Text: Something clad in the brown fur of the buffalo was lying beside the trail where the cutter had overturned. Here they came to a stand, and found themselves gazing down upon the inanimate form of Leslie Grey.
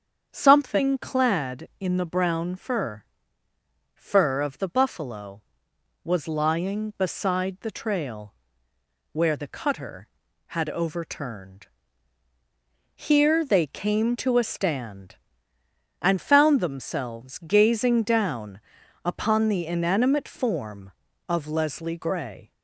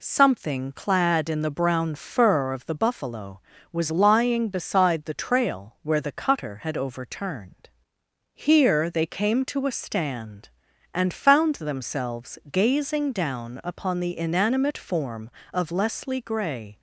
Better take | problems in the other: second | starts louder than the rest; strong; until 1.3 s; 7.5 dB // says "fur" twice; at 3.9 s // pauses between "trail" and "where"; noticeable; at 8.3 s; 0.78 s long // pauses between "down" and "upon"; at 18.5 s; 0.44 s long

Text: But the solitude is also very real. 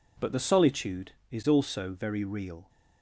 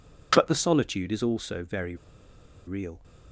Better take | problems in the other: first | pauses between "very" and "real"; noticeable; at 1.9 s; 0.71 s long

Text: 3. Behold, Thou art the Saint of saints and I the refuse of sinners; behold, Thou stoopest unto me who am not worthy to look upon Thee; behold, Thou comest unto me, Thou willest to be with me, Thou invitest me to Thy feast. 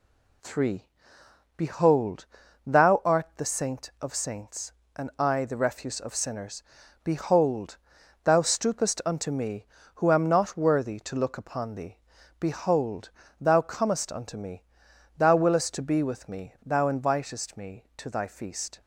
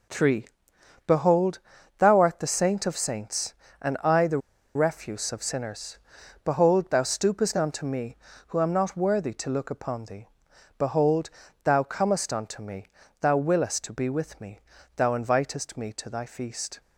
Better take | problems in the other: first | pauses between "the" and "refuse"; at 4.3 s; 0.37 s long

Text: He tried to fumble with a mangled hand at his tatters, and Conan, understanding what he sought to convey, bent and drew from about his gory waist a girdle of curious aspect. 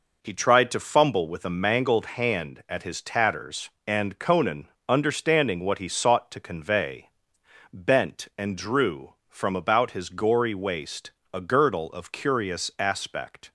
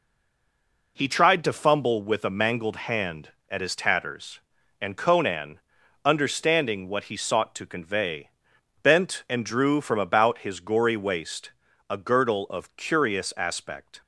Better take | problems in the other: first | stays silent before the first word; slight; until 0.9 s; 0.9 s long // pauses between "waist" and "a"; slight; at 11.5 s; 0.36 s long; slight in the first

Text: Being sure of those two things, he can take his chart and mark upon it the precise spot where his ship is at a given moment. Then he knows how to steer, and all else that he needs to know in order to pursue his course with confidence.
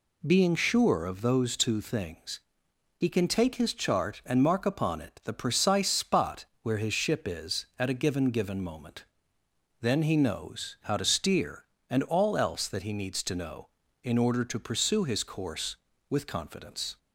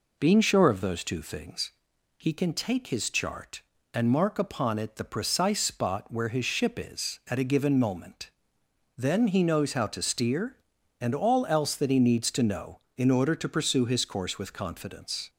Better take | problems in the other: second | pauses between "spot" and "where"; slight; at 6.4 s; 0.18 s long // says "given" twice; at 8.2 s

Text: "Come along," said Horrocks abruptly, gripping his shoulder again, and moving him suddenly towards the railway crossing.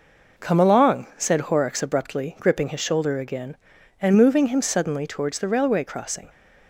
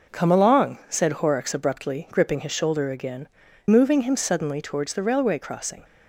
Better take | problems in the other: first | skips "and"; at 3.4 s

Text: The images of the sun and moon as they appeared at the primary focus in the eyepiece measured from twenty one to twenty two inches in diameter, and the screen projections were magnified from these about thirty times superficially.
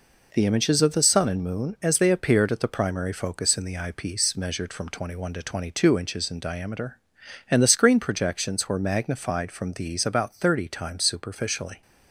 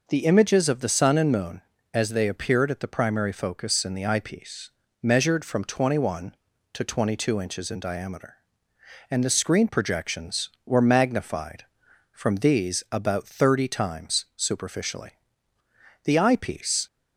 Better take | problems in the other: first | pauses between "eyepiece" and "measured"; slight; at 4.7 s; 0.32 s long // goes on to say "The eyepiece"; noticeable; from 16.0 s on; 0.82 s long

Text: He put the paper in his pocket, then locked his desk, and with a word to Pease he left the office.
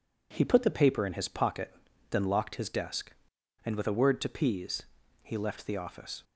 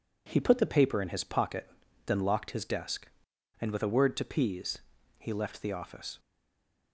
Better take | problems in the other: first | pauses between "Pease" and "he"; at 4.7 s; 0.38 s long; also in the first // stays silent after the last word; slight; from 6.1 s on; 0.8 s long

